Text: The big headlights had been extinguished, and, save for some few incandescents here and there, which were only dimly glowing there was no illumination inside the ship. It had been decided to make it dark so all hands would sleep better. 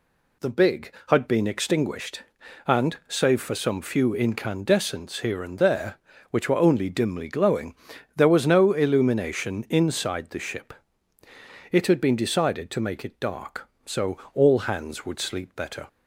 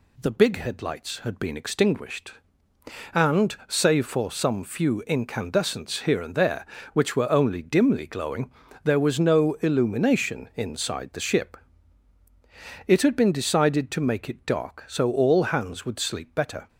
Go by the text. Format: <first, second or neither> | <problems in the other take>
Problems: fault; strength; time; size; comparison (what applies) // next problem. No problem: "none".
second | skips "headlights"; at 0.9 s // pauses between "glowing" and "there"; at 7.7 s; 0.42 s long; slight in the second // pauses between "so" and "all"; slight; at 14.1 s; 0.16 s long